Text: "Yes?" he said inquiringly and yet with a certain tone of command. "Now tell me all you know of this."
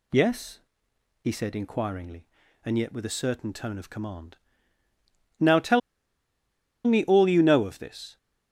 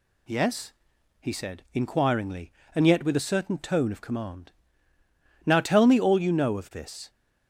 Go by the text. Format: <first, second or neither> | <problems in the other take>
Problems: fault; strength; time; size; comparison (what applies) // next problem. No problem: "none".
second | pauses between "tell" and "me"; at 5.8 s; 1.0 s long